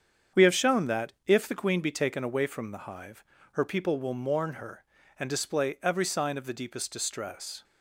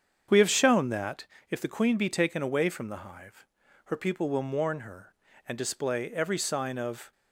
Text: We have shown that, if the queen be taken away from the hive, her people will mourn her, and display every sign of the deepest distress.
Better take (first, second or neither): first